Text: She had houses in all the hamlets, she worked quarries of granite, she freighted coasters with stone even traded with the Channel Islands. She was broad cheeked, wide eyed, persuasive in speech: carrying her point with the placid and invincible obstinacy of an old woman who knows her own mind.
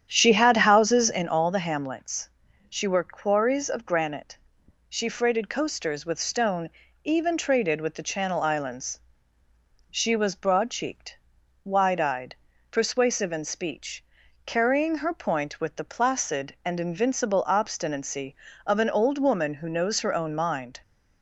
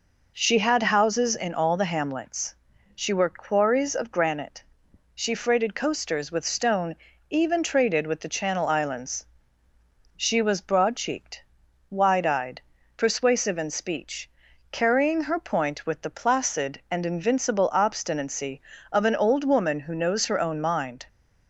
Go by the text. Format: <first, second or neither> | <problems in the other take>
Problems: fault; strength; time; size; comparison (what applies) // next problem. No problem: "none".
second | starts louder than the rest; strong; until 1.5 s; 9 dB // pauses between "stone" and "even"; slight; at 6.6 s; 0.34 s long; slight in the second